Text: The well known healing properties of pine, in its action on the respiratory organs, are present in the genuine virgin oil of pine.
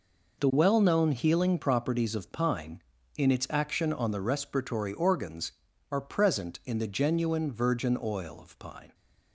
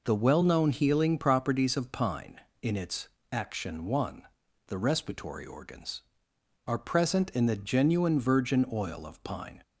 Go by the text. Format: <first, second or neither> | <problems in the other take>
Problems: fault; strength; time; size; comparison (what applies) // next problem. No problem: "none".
first | pauses between "its" and "action"; slight; at 3.0 s; 0.24 s long // says "one" for "on"; at 3.8 s